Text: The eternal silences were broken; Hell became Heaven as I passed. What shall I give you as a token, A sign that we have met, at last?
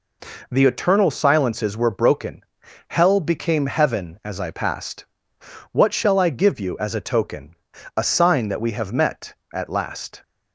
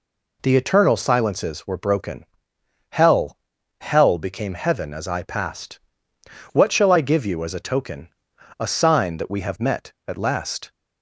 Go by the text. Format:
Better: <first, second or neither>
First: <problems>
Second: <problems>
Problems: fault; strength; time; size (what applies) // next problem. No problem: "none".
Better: first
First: none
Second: says "Hell" twice; at 3.8 s